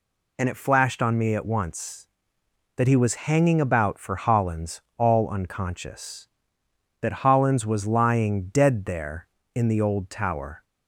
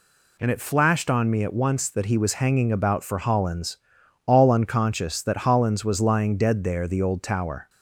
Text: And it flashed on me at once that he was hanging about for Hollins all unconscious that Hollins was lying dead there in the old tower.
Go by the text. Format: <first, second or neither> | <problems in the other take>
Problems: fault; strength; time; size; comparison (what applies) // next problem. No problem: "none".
first | pauses between "Hollins" and "all"; noticeable; at 3.7 s; 0.48 s long; slight in the first // skips "in"; at 6.8 s